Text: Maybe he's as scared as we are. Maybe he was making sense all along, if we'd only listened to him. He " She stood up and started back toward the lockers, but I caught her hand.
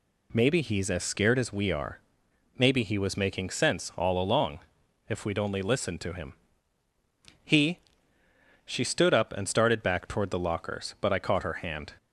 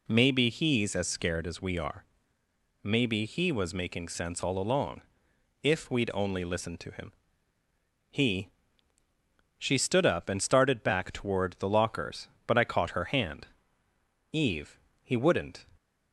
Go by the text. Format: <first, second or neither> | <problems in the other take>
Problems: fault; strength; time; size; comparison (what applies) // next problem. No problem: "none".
first | goes on to say "Eve he wouldn't"; from 14.3 s on; 1.3 s long